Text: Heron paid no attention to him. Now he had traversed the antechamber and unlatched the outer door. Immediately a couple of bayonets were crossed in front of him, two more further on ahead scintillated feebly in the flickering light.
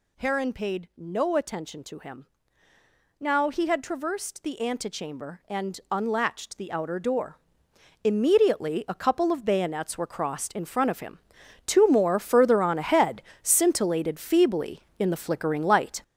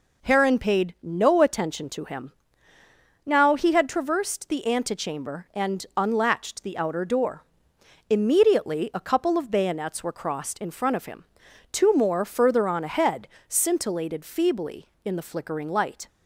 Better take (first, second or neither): second